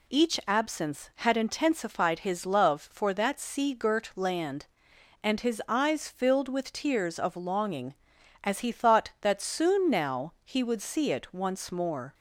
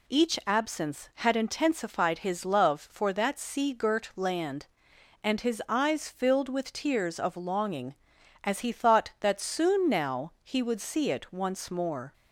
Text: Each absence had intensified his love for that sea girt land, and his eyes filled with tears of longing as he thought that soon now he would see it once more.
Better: neither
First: none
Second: none

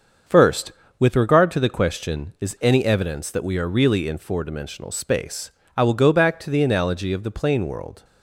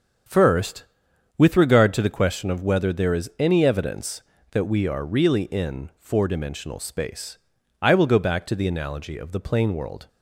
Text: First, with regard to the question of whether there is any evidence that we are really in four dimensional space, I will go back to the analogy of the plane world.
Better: second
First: starts louder than the rest; until 1.5 s; 6.5 dB // skips "of whether there"; at 2.3 s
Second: starts louder than the rest; strong; until 1.8 s; 7.5 dB

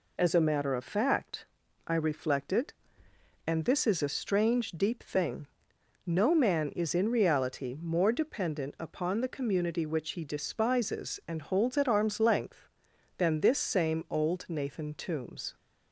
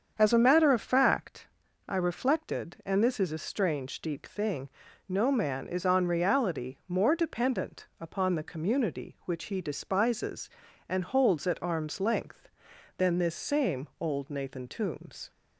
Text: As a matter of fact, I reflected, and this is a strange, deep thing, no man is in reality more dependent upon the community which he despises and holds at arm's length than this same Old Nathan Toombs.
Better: first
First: none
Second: starts louder than the rest; strong; until 1.1 s; 7.5 dB // says "on" for "in"; at 5.8 s

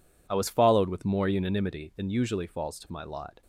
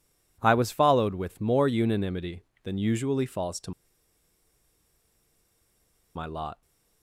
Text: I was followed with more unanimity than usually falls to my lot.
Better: first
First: none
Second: pauses between "to" and "my"; strong; at 3.7 s; 2.4 s long

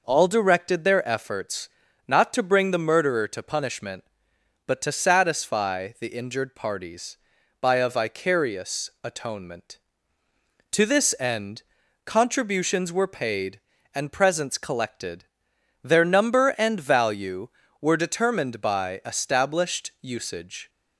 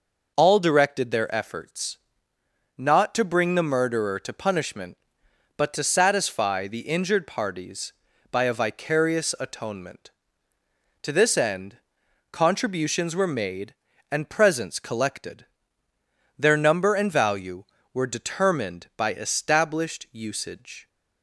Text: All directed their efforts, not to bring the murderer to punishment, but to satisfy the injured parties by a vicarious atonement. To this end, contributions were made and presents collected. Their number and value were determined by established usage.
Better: second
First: says "paid" for "made"; at 13.0 s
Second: none

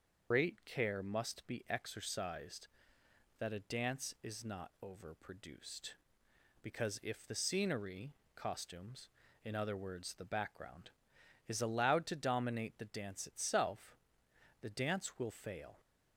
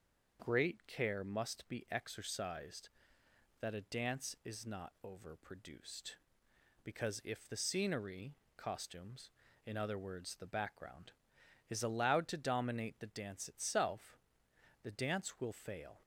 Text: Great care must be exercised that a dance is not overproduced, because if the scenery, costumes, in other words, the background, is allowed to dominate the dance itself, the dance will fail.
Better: second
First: loses the start of "Great"; at 0.3 s; 125 ms // starts louder than the rest; noticeable; until 1.3 s; 6 dB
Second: none

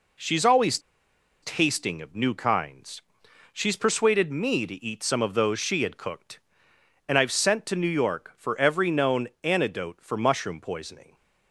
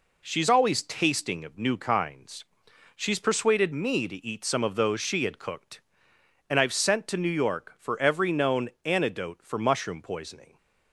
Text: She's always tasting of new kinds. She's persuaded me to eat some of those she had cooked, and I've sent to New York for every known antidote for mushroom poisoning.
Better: second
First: pauses between "always" and "tasting"; noticeable; at 0.7 s; 0.63 s long // pauses between "known" and "antidote"; slight; at 9.2 s; 0.16 s long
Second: pauses between "known" and "antidote"; slight; at 8.6 s; 0.16 s long

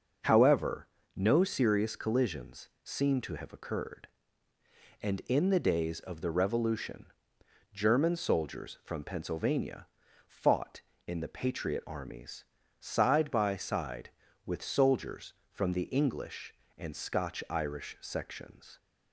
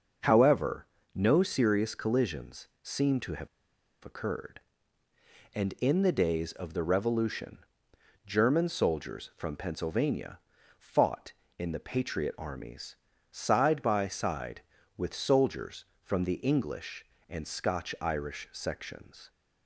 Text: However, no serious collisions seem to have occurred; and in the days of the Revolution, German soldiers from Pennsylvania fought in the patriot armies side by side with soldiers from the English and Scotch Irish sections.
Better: first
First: starts louder than the rest; noticeable; until 1.5 s; 6 dB // pauses between "collisions" and "seem"; slight; at 2.6 s; 0.16 s long // pauses between "Pennsylvania" and "fought"; at 9.8 s; 0.39 s long // pauses between "armies" and "side"; slight; at 12.4 s; 0.36 s long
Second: starts louder than the rest; noticeable; until 1.5 s; 6 dB // pauses between "collisions" and "seem"; slight; at 2.6 s; 0.16 s long // pauses between "have" and "occurred"; noticeable; at 3.4 s; 0.55 s long // pauses between "Pennsylvania" and "fought"; at 10.3 s; 0.38 s long // pauses between "armies" and "side"; slight; at 12.9 s; 0.36 s long

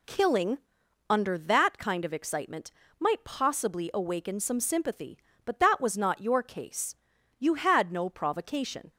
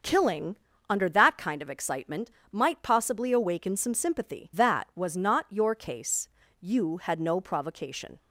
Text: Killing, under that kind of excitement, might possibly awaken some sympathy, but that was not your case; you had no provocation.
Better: first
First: none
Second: starts louder than the rest; until 1.3 s; 6.5 dB // skips "but"; at 4.5 s

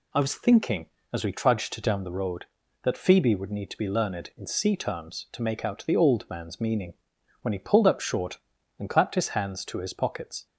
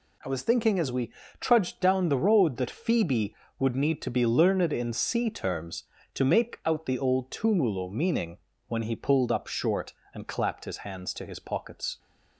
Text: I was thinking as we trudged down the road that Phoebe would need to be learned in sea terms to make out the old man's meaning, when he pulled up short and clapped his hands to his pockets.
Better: first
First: none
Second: pauses between "we" and "trudged"; slight; at 1.1 s; 0.26 s long // says "tumulo" for "man's"; at 7.3 s

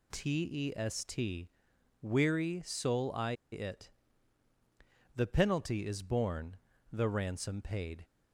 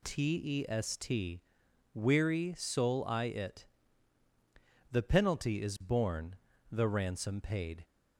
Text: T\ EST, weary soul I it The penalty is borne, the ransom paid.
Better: second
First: pauses between "I" and "it"; slight; at 3.3 s; 0.18 s long // pauses between "it" and "The"; strong; at 3.8 s; 1.2 s long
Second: pauses between "it" and "The"; strong; at 3.6 s; 1.2 s long

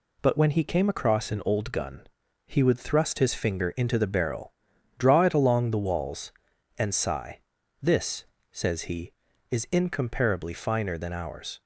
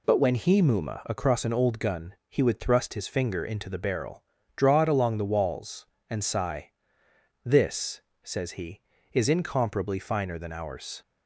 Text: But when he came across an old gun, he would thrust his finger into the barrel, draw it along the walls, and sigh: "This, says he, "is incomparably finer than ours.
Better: first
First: none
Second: says "muma" for "came"; at 0.6 s

